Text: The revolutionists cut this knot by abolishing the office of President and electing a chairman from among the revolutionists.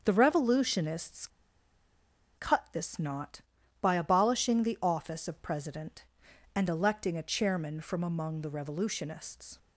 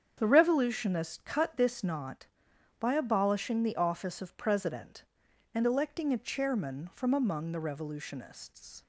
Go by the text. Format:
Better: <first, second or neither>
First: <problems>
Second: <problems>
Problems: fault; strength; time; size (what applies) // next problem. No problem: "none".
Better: second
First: starts louder than the rest; strong; until 1.0 s; 7 dB // pauses between "revolutionists" and "cut"; at 1.2 s; 1.0 s long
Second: starts louder than the rest; strong; until 1.1 s; 8 dB